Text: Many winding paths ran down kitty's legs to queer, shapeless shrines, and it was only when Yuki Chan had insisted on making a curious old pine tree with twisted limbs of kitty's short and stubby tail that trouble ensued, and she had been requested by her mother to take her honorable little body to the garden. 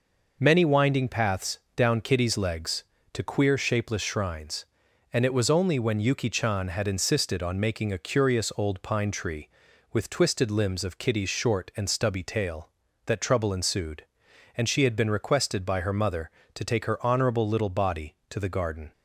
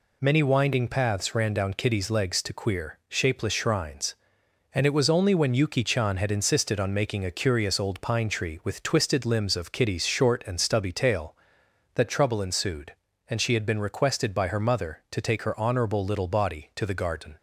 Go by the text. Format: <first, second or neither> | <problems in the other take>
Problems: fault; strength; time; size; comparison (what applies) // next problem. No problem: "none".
second | skips "ran"; at 1.6 s